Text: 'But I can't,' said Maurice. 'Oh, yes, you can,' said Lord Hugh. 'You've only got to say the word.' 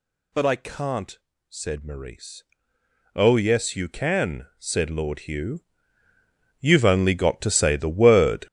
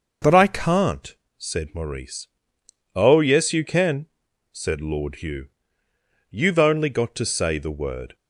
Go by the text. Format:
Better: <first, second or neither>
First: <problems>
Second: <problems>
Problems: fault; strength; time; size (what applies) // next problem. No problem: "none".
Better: second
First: gets louder; strong; throughout; 10 dB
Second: none